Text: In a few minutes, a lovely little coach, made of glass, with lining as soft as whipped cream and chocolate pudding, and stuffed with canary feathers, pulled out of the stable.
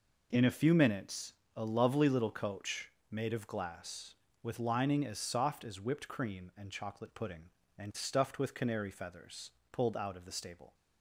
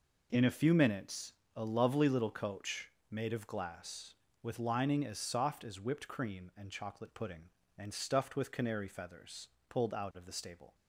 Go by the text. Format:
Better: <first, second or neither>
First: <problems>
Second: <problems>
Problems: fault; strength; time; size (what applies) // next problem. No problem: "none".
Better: neither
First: none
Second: none